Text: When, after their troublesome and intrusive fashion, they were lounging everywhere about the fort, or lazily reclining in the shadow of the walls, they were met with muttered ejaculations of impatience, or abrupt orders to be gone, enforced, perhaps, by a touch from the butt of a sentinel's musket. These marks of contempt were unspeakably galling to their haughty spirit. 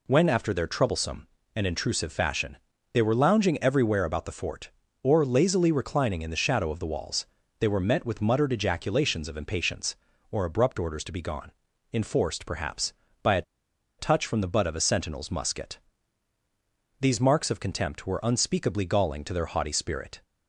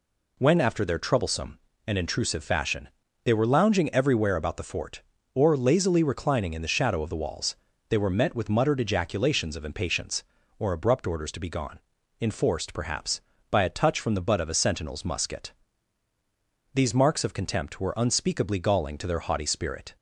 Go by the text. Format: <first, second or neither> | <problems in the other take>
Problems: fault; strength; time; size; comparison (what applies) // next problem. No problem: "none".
second | pauses between "a" and "touch"; noticeable; at 13.4 s; 0.56 s long